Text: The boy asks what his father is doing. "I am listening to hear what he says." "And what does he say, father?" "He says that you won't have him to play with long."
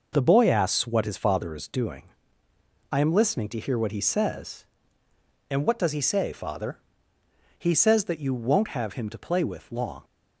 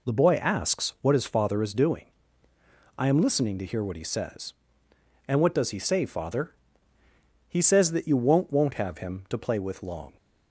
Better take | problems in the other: first | says "won't" twice; at 8.4 s

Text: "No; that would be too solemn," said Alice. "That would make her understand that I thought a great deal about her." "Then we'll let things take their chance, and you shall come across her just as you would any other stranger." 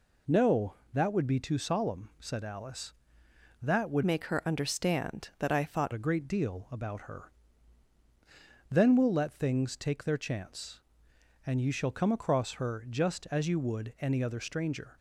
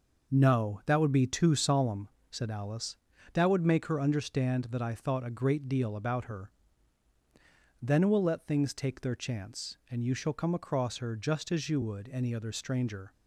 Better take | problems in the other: second | changes voice from "make" to "thought"; from 4.0 to 5.9 s; 1.9 s long

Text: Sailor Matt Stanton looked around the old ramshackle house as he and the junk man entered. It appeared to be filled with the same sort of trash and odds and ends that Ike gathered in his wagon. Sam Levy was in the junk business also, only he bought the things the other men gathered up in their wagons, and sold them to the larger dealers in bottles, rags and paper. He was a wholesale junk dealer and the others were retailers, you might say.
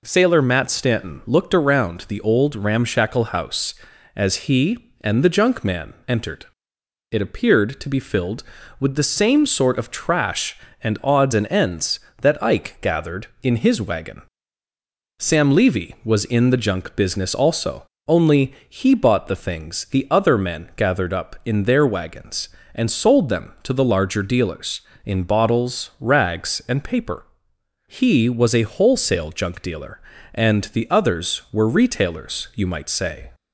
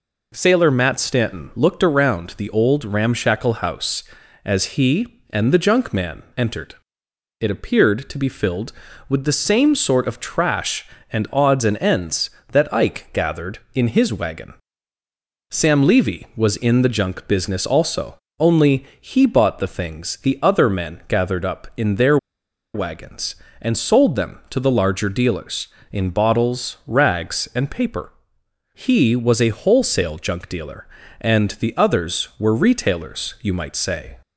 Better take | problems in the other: first | pauses between "their" and "wagons"; noticeable; at 22.1 s; 0.57 s long

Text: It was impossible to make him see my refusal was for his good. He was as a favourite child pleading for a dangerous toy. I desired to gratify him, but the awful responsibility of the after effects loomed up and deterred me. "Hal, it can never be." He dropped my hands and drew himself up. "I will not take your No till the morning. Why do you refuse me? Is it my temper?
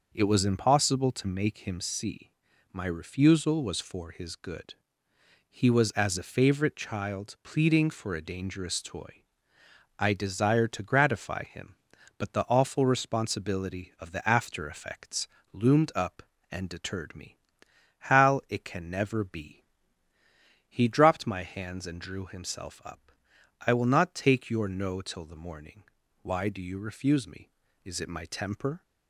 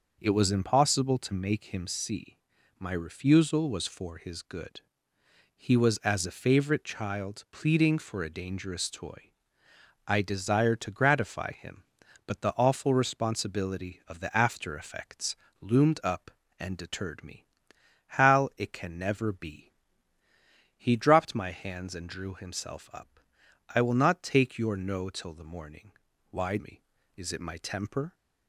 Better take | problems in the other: first | pauses between "see" and "my"; at 2.3 s; 0.40 s long; also in the first // pauses between "effects" and "loomed"; slight; at 15.3 s; 0.26 s long; slight in the first // skips "do you refuse"; at 26.5 s

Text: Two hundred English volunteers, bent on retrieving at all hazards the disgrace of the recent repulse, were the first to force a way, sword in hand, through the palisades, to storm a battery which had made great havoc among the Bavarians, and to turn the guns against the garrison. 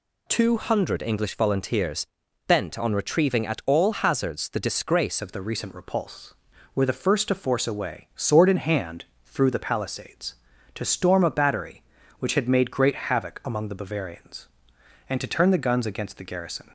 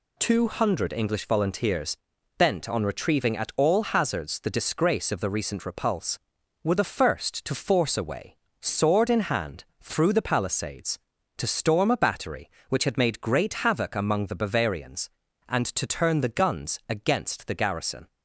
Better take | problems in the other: second | changes voice at "of"; from 5.2 s on; 11.5 s long

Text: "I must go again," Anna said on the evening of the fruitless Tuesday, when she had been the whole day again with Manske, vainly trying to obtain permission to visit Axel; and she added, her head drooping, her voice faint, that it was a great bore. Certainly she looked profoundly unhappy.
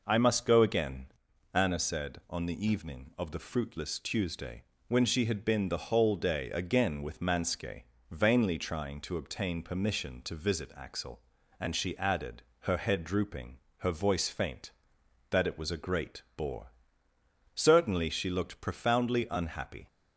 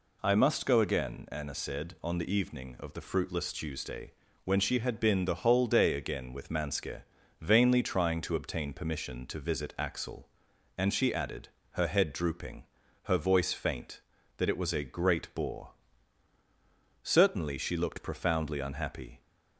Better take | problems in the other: neither | none

